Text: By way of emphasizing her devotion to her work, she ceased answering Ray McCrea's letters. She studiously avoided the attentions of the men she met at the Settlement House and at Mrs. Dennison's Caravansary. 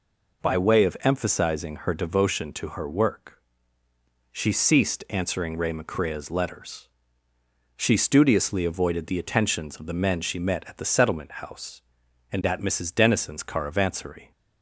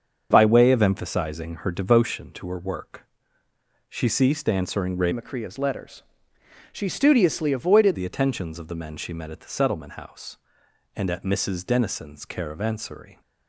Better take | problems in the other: first | starts louder than the rest; until 1.3 s; 7 dB // changes voice from "McCrea's" to "avoided"; from 5.1 to 7.9 s; 2.8 s long

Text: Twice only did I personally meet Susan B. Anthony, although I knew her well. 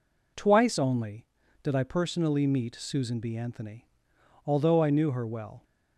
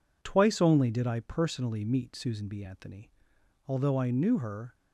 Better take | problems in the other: first | stops before "well"; at 4.7 s

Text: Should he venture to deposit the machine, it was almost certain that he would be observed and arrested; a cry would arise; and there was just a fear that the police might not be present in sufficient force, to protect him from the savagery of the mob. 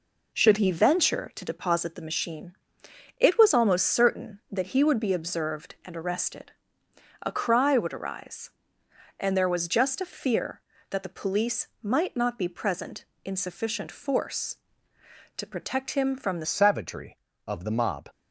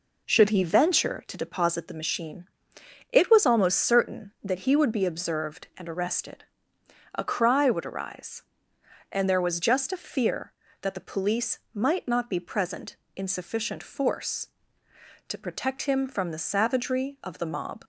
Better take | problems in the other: second | pauses between "police" and "might"; slight; at 11.6 s; 0.16 s long; slight in the second // changes voice at "savagery"; from 16.4 s on; 1.6 s long

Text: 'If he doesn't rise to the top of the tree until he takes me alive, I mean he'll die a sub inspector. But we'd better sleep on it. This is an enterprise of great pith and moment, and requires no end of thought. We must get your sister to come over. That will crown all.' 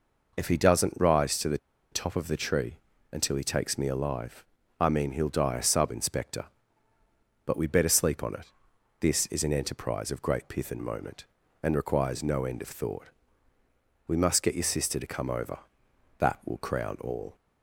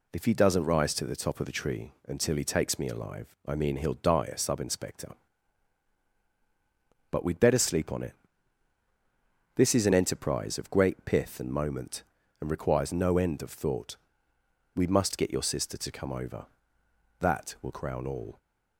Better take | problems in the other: second | pauses between "the" and "top"; slight; at 1.5 s; 0.34 s long // pauses between "tree" and "until"; slight; at 2.7 s; 0.34 s long

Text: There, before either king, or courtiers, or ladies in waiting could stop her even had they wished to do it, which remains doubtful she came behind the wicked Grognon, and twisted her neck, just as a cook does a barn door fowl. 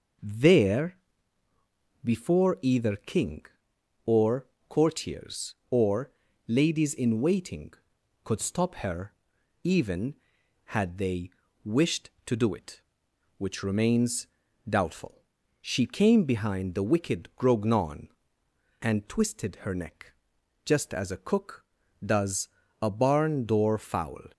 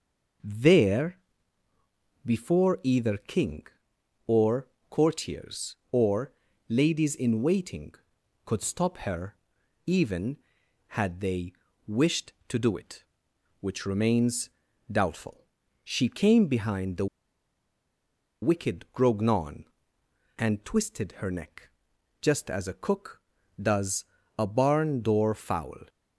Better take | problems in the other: first | pauses between "or" and "courtiers"; slight; at 4.6 s; 0.22 s long; slight in the first // pauses between "or" and "ladies"; slight; at 6.3 s; 0.36 s long; slight in the first // pauses between "her" and "even"; noticeable; at 9.3 s; 0.52 s long; noticeable in the first // pauses between "they" and "wished"; slight; at 11.5 s; 0.34 s long; slight in the first // pauses between "remains" and "doubtful"; at 14.4 s; 0.40 s long; also in the first // pauses between "doubtful" and "she"; at 15.4 s; 0.40 s long; also in the first // pauses between "the" and "wicked"; strong; at 17.0 s; 1.3 s long // pauses between "does" and "a"; slight; at 24.0 s; 0.36 s long; slight in the first

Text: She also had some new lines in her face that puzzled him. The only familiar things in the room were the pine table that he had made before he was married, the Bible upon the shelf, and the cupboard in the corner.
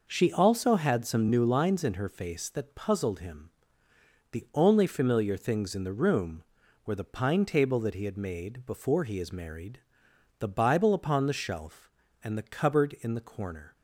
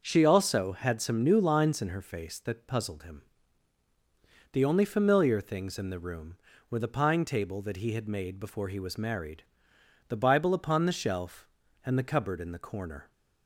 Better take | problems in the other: second | says "is" for "was"; at 9.1 s

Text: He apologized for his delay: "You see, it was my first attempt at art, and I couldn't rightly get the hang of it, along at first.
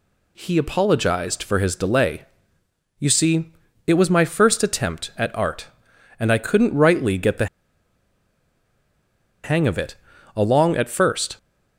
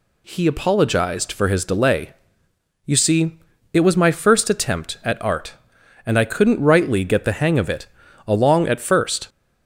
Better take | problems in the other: second | pauses between "the" and "hang"; strong; at 7.4 s; 1.9 s long

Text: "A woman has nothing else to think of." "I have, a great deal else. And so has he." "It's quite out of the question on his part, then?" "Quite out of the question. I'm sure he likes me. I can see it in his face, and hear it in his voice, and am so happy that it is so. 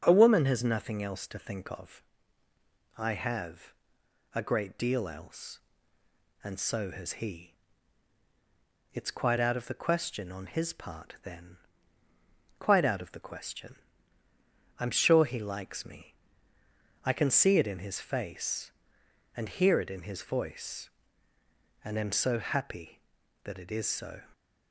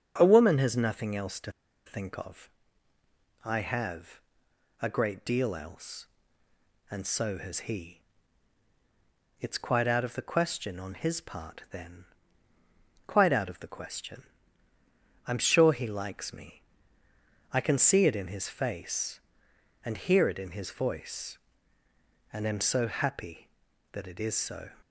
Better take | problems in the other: first | starts louder than the rest; until 1.1 s; 6.5 dB; also in the first // pauses between "to" and "think"; slight; at 1.5 s; 0.35 s long

